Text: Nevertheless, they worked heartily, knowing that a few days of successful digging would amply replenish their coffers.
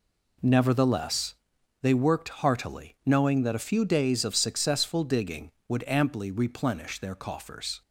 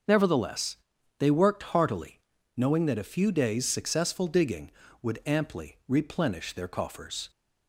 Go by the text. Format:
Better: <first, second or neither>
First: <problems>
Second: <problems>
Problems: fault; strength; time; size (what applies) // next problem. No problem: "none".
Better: first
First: none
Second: starts louder than the rest; until 1.5 s; 6.5 dB // skips "of"; at 3.6 s